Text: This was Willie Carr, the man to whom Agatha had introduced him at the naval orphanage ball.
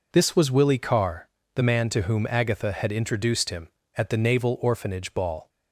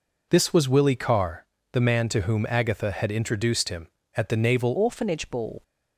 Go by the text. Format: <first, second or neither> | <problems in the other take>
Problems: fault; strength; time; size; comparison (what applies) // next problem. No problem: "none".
first | changes voice at "orphanage"; from 4.7 s on; 0.9 s long